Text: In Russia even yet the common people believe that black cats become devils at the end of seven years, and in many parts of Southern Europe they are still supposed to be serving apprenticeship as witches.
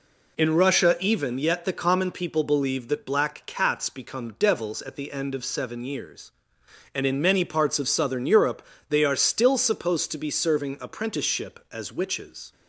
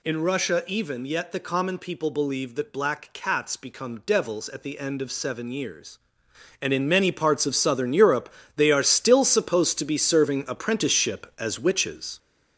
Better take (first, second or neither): first